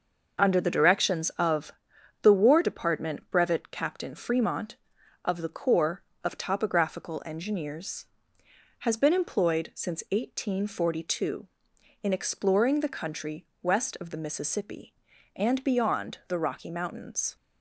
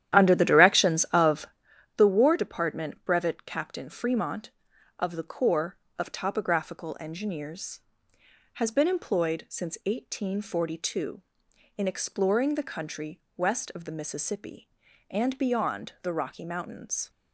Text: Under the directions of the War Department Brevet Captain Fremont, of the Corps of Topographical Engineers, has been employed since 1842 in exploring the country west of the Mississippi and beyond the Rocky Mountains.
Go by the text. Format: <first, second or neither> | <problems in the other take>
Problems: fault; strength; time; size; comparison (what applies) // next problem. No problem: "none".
first | starts louder than the rest; strong; until 1.7 s; 11 dB // pauses between "of" and "the"; noticeable; at 1.4 s; 0.48 s long; noticeable in the first // pauses between "country" and "west"; slight; at 13.1 s; 0.16 s long; slight in the first